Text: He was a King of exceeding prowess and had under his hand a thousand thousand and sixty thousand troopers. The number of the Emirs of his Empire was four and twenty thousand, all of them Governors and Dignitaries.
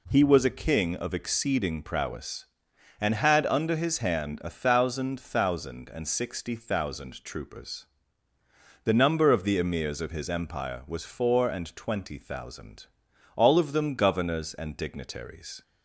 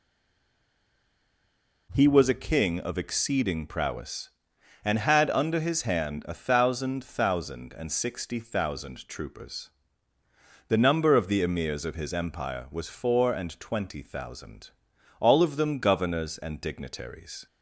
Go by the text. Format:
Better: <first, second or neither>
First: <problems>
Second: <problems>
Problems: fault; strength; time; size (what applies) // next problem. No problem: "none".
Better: first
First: none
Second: stays silent before the first word; noticeable; until 1.9 s; 1.9 s long